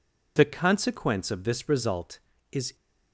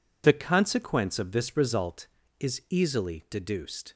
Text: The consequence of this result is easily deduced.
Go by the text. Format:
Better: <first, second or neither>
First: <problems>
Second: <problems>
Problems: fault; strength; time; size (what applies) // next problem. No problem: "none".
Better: second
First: stops before "easily deduced"; at 2.7 s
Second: none